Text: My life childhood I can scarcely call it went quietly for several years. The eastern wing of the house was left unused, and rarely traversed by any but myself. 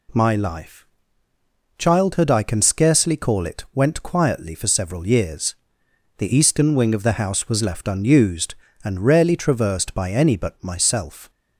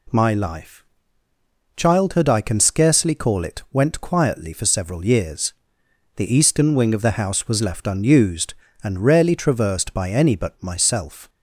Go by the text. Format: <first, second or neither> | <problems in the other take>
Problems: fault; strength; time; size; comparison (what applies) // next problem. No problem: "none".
neither | pauses between "life" and "childhood"; noticeable; the same in both